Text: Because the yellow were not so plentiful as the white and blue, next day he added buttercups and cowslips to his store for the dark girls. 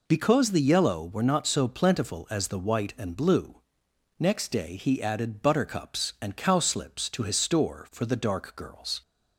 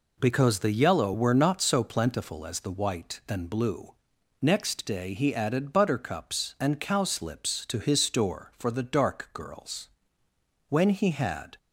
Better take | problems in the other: first | goes on to say "When he had"; noticeable; from 10.6 s on; 0.88 s long

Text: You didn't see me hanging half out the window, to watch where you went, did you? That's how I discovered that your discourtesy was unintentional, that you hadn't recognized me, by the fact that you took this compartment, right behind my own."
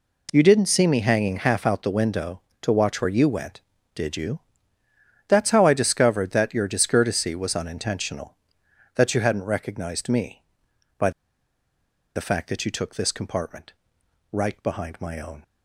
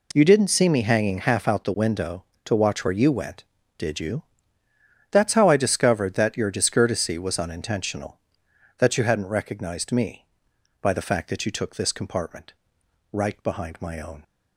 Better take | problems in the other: second | pauses between "by" and "the"; at 11.0 s; 1.0 s long

